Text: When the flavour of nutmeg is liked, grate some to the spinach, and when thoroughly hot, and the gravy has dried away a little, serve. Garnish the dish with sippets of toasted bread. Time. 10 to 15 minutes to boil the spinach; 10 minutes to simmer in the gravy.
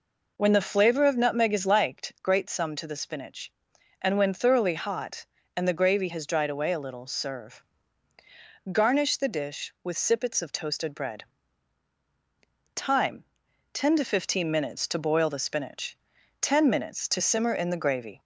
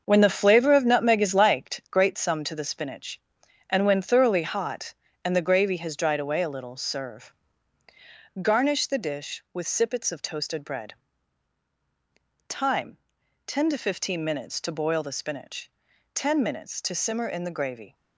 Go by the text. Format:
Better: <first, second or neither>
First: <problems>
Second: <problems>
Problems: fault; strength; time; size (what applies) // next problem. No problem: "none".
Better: first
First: none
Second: gets quieter; strong; throughout; 8 dB